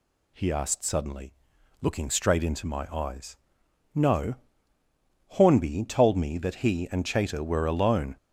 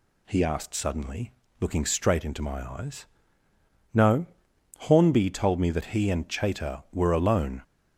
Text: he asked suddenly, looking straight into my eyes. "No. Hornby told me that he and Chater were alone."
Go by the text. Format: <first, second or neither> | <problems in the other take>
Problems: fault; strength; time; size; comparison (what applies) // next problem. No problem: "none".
neither | none